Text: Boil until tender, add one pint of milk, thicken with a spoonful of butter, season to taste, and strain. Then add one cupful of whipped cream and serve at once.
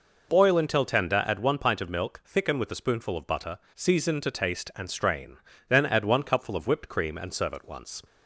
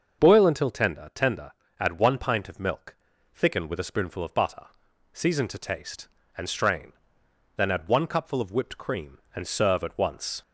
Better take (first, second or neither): first